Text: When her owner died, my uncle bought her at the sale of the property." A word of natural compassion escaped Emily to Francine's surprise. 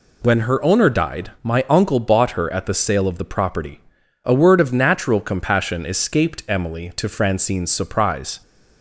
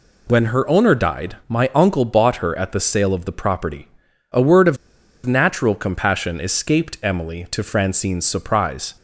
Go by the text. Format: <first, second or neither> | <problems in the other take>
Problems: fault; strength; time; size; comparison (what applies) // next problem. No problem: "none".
first | pauses between "of" and "natural"; noticeable; at 4.7 s; 0.48 s long